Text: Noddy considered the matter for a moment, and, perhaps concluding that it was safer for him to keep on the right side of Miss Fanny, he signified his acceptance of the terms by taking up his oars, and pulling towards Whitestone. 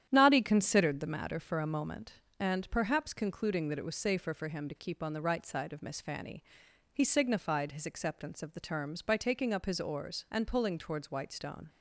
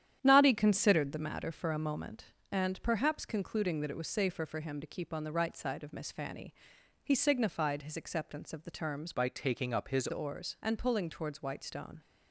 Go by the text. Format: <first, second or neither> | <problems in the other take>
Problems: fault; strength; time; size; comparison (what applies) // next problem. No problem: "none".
first | starts louder than the rest; strong; until 1.2 s; 10 dB; strong in the first // changes voice from "by" to "his"; from 9.1 to 10.0 s; 0.9 s long